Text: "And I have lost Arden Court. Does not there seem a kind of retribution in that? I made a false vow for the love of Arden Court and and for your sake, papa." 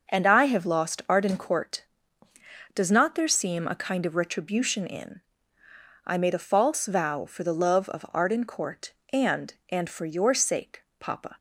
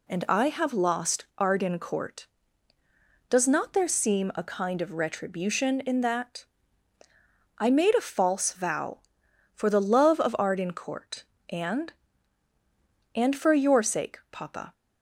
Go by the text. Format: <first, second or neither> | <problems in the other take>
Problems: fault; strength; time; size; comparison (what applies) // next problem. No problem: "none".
second | skips "that"; at 5.6 s